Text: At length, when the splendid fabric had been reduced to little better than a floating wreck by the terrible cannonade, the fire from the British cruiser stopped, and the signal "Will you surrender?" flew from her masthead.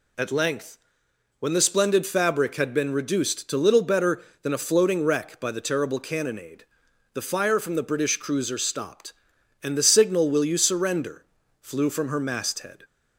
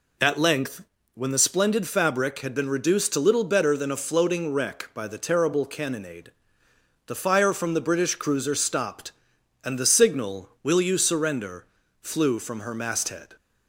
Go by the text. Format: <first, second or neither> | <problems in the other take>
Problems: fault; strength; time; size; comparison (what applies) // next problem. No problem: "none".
neither | none